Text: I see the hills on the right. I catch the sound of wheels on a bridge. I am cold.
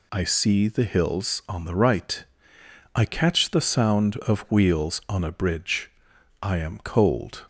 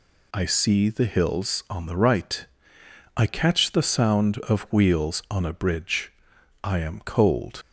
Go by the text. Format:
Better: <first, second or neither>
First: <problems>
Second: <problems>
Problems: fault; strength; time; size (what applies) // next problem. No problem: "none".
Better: first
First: none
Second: leaves "cold" unfinished; at 7.6 s; 60 ms